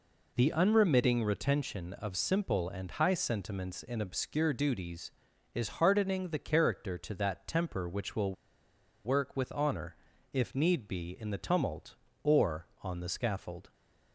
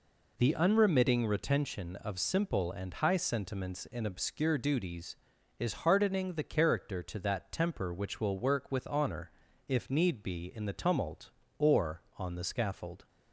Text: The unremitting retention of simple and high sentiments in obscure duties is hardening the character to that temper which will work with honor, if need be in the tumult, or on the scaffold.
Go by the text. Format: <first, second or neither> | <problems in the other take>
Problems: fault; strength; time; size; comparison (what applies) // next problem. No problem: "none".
second | pauses between "will" and "work"; noticeable; at 8.3 s; 0.71 s long